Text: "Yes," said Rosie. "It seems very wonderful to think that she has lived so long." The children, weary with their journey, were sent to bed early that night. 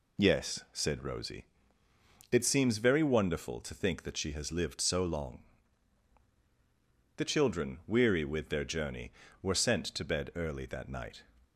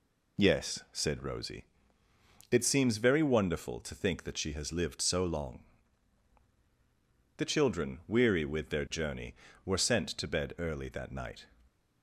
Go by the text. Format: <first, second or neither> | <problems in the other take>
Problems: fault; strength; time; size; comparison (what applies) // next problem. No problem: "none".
neither | none